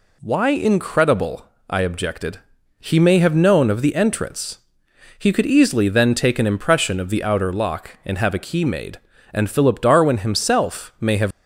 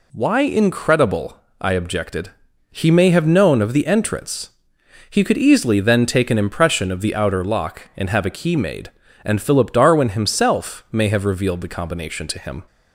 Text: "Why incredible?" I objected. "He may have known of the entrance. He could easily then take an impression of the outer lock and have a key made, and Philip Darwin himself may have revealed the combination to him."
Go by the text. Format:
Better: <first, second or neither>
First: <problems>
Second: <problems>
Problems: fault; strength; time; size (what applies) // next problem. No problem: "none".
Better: second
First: stops before "revealed the combination to him"; at 11.3 s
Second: none